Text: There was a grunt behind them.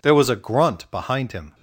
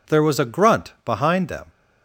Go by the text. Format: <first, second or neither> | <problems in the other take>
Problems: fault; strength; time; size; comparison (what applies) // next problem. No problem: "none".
second | says "him" for "them"; at 1.3 s